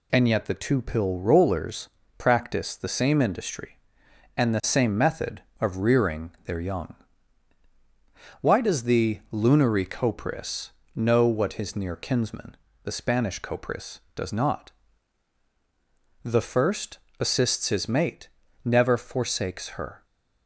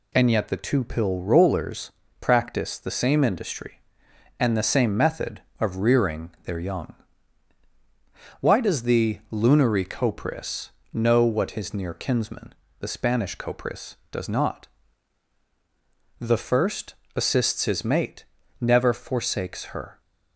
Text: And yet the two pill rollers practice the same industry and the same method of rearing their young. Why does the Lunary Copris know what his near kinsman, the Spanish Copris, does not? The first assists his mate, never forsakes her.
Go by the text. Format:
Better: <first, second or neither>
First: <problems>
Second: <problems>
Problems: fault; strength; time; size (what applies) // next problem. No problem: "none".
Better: neither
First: pauses between "rollers" and "practice"; slight; at 1.8 s; 0.28 s long // pauses between "Copris" and "know"; slight; at 10.7 s; 0.26 s long // pauses between "first" and "assists"; slight; at 16.9 s; 0.22 s long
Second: pauses between "rollers" and "practice"; slight; at 1.9 s; 0.28 s long // pauses between "Copris" and "know"; slight; at 10.6 s; 0.24 s long // pauses between "first" and "assists"; slight; at 16.9 s; 0.22 s long